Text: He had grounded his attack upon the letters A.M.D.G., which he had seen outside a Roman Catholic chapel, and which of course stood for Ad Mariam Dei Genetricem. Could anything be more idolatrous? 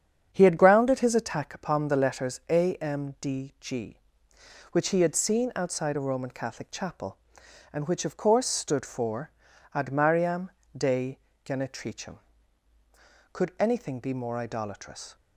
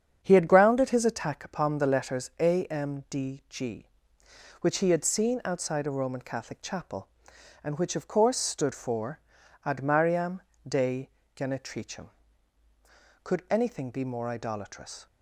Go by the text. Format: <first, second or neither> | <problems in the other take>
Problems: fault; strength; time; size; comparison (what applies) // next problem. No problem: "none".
neither | starts louder than the rest; strong; the same in both // pauses between "for" and "Ad"; the same in both // pauses between "Mariam" and "Dei"; slight; the same in both // pauses between "Dei" and "Genetricem"; slight; the same in both